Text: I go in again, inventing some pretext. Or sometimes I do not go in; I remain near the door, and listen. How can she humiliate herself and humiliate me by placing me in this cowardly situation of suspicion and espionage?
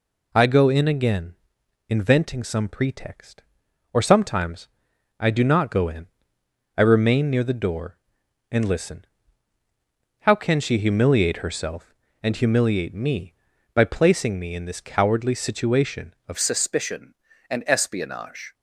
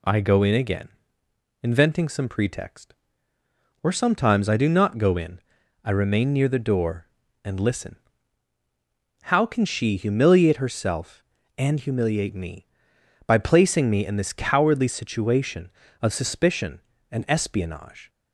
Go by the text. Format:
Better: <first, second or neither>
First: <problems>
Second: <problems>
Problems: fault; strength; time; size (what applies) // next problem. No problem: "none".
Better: second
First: pauses between "sometimes" and "I"; noticeable; at 4.6 s; 0.50 s long // changes voice at "suspicion"; from 16.3 s on; 2.2 s long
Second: none